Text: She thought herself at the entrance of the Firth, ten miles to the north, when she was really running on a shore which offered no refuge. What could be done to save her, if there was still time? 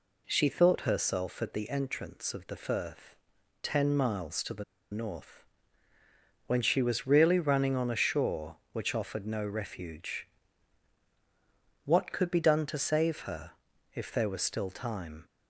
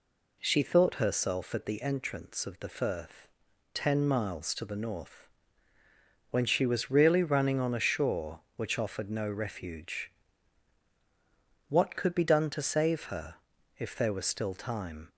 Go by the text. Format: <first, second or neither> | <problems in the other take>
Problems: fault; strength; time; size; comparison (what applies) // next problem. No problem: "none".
second | pauses between "the" and "north"; slight; at 4.6 s; 0.28 s long